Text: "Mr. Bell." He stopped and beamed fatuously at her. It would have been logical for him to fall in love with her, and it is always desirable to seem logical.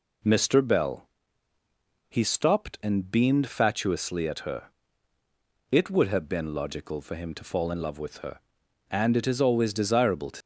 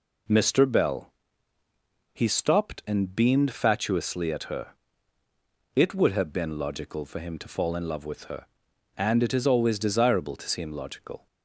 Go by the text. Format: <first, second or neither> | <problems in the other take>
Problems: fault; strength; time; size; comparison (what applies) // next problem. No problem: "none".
second | stops before "seem logical"; at 10.4 s